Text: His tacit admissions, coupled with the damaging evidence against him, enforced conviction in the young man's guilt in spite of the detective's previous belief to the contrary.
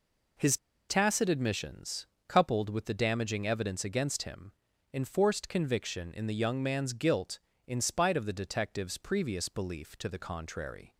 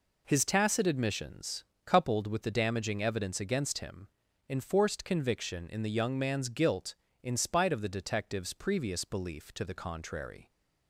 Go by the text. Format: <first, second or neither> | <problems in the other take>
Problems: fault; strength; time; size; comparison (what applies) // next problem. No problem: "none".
second | pauses between "His" and "tacit"; slight; at 0.5 s; 0.33 s long